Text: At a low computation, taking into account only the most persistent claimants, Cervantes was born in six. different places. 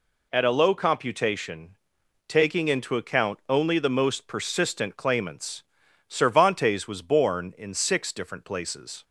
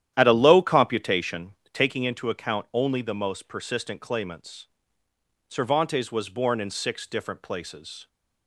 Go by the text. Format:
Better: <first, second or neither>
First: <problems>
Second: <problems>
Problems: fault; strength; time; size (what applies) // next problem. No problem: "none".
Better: first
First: none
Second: starts louder than the rest; strong; until 2.1 s; 11 dB